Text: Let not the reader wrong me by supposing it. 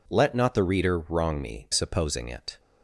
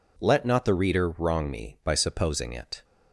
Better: second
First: skips "by"; at 1.6 s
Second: none

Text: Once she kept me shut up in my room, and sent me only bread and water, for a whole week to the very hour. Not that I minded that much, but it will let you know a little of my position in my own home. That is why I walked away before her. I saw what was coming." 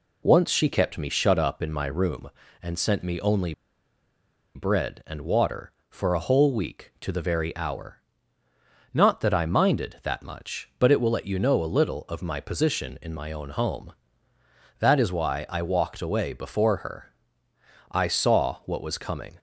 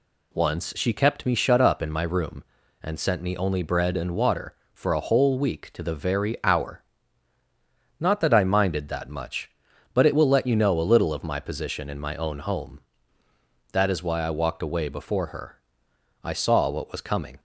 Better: second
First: pauses between "only" and "bread"; at 3.5 s; 1.0 s long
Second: none

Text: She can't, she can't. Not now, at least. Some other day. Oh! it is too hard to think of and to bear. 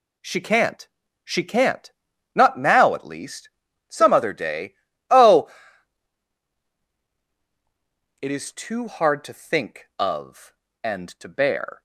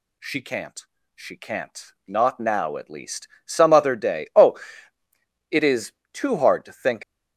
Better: first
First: none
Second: pauses between "is" and "too"; slight; at 5.9 s; 0.18 s long // stops before "of and to bear"; at 7.0 s

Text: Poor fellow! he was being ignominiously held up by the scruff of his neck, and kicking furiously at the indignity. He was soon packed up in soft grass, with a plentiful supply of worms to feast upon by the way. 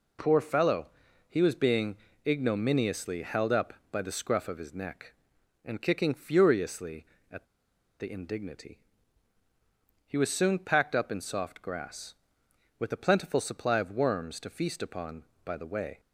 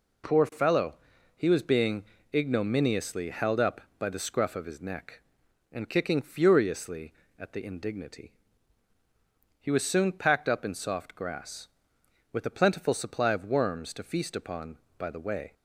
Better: second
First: pauses between "being" and "ignominiously"; slight; at 1.9 s; 0.30 s long // pauses between "at" and "the"; noticeable; at 7.4 s; 0.54 s long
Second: pauses between "being" and "ignominiously"; slight; at 2.0 s; 0.30 s long

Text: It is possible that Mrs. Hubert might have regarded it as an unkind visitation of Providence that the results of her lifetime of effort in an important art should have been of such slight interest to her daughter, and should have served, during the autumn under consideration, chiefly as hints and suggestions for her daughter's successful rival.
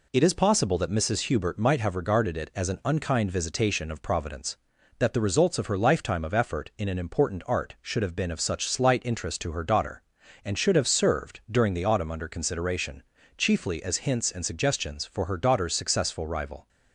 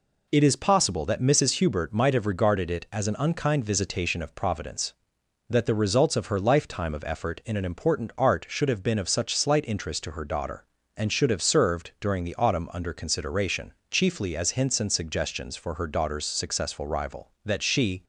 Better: first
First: none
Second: goes on to say "That she"; from 17.4 s on; 0.58 s long

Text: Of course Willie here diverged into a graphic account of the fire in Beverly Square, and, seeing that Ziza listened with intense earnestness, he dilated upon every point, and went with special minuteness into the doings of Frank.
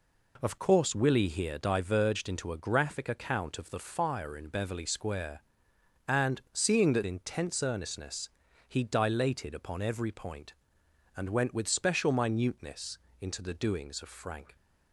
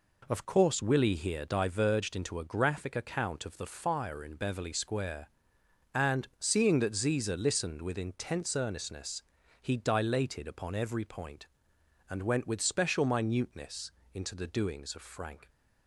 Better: second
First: skips "Ziza listened with"; at 7.0 s // pauses between "minuteness" and "into"; slight; at 12.9 s; 0.24 s long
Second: pauses between "minuteness" and "into"; slight; at 13.9 s; 0.24 s long

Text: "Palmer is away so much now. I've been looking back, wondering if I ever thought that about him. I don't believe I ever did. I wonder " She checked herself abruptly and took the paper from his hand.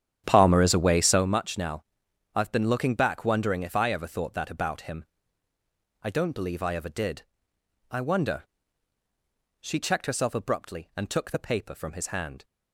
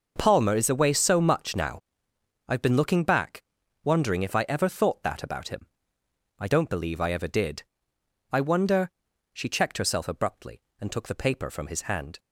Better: second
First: starts louder than the rest; strong; until 1.3 s; 10 dB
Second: none

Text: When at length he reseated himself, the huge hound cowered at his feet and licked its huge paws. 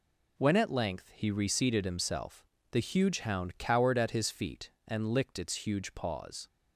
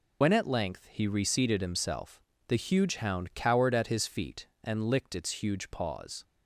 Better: first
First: none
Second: loses the start of "When"; at 0.2 s; 60 ms

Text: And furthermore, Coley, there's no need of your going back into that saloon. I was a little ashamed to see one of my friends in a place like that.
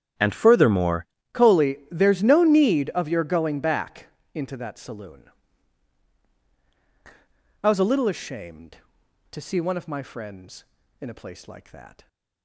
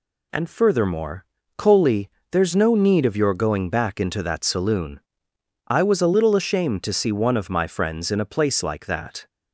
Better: second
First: starts louder than the rest; strong; until 1.4 s; 9.5 dB // changes voice at "Coley"; from 1.3 s on; 10.7 s long // pauses between "back" and "into"; slight; at 4.0 s; 0.26 s long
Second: none

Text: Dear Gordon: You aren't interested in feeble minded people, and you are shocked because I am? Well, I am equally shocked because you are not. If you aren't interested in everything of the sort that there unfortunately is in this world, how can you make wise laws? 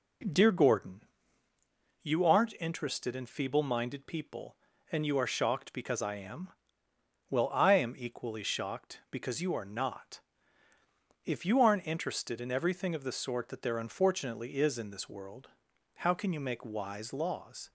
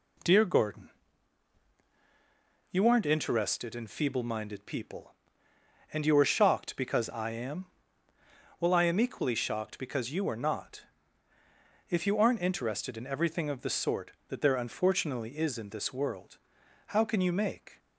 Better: first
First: none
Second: stops before "wise laws"; at 17.7 s

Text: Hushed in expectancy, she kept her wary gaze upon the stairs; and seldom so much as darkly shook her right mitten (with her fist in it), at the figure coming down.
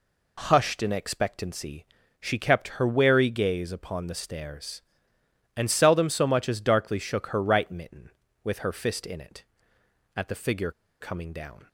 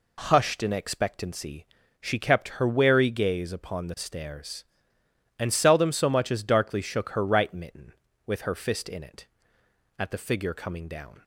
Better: second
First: pauses between "figure" and "coming"; slight; at 10.7 s; 0.30 s long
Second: none

